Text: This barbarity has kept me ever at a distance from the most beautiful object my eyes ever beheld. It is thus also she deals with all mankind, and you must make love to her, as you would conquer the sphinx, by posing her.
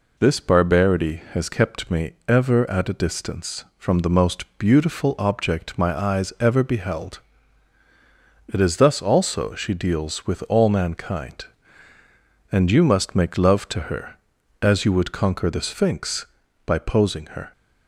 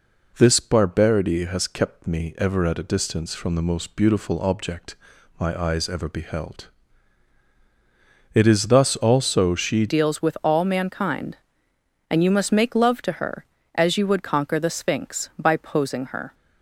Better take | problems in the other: first | pauses between "object" and "my"; at 4.9 s; 0.42 s long // changes voice at "deals"; from 9.8 s on; 6.5 s long

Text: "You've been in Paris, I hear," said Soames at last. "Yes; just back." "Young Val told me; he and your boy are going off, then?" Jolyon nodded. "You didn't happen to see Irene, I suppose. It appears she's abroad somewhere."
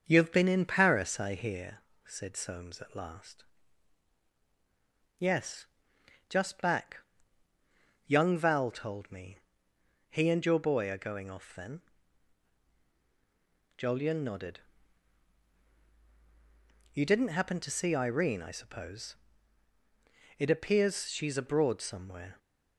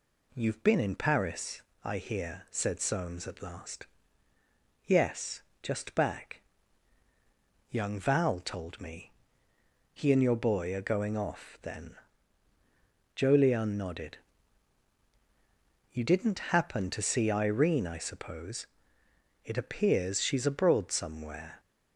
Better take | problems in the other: second | starts louder than the rest; until 1.6 s; 6.5 dB

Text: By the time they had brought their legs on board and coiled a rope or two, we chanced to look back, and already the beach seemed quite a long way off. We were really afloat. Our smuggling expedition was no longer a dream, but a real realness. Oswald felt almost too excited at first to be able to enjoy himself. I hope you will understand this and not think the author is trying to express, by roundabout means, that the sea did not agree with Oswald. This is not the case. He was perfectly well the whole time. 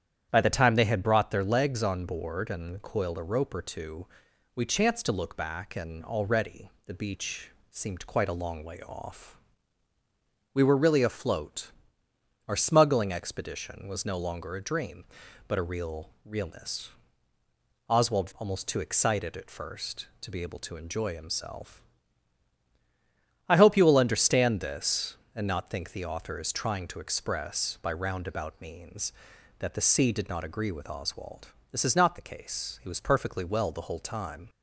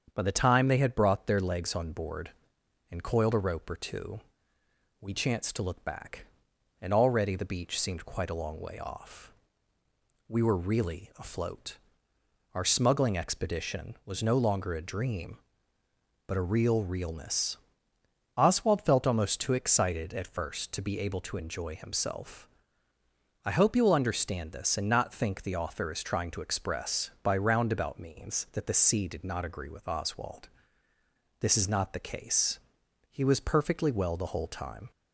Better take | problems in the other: second | starts louder than the rest; strong; until 1.3 s; 9.5 dB; strong in the second // pauses between "already" and "the"; slight; at 6.6 s; 0.16 s long // pauses between "beach" and "seemed"; slight; at 7.4 s; 0.20 s long // skips "felt"; at 18.3 s

